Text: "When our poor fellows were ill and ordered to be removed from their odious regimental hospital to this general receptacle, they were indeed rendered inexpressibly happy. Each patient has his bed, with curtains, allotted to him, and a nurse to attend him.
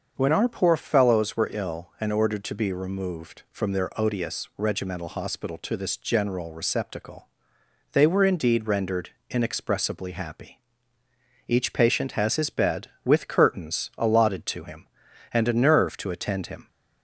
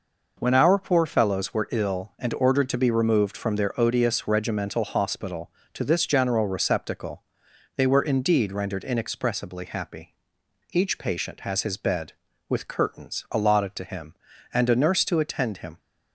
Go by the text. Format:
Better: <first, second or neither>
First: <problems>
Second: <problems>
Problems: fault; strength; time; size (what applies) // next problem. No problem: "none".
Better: second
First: starts louder than the rest; until 1.1 s; 6.5 dB // pauses between "rendered" and "inexpressibly"; slight; at 9.1 s; 0.18 s long // says "nerve" for "nurse"; at 15.5 s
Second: none